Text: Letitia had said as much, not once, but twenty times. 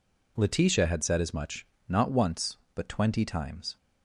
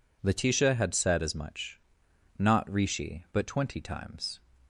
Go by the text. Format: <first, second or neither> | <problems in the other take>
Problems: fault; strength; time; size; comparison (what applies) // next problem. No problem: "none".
first | says "rishi" for "once"; at 2.6 s